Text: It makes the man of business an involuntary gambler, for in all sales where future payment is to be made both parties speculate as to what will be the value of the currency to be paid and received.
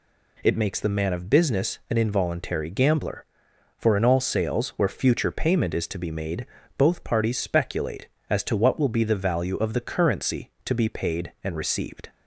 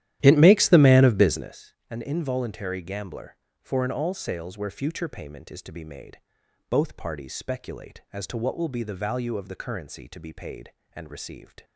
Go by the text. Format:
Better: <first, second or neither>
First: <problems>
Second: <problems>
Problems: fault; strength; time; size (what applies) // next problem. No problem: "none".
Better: first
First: pauses between "made" and "both"; slight; at 6.4 s; 0.32 s long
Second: starts louder than the rest; strong; until 1.5 s; 12.5 dB // pauses between "business" and "an"; slight; at 1.7 s; 0.16 s long // pauses between "made" and "both"; noticeable; at 6.1 s; 0.50 s long